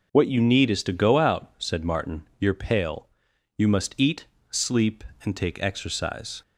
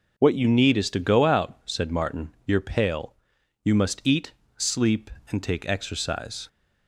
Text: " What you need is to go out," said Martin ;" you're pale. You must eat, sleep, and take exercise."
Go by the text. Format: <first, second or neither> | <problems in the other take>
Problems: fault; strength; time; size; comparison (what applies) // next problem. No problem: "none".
neither | none